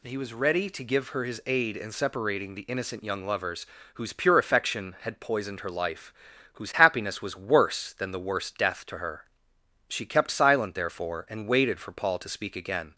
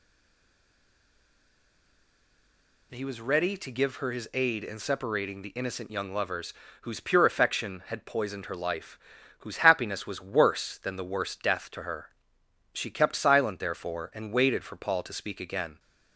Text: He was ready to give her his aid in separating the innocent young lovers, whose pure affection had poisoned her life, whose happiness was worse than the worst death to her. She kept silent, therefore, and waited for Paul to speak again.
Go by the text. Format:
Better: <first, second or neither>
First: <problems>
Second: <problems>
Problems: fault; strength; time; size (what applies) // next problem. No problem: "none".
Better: first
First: none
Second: stays silent before the first word; strong; until 2.9 s; 2.9 s long